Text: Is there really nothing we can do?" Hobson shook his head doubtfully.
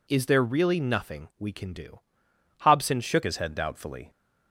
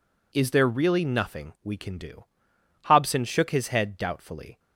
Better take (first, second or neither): second